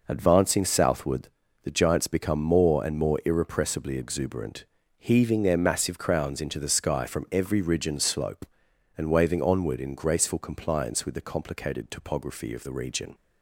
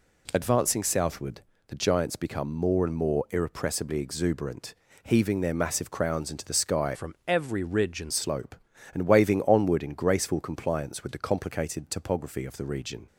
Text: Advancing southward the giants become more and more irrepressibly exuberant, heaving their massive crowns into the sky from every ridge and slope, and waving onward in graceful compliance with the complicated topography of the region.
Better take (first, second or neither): first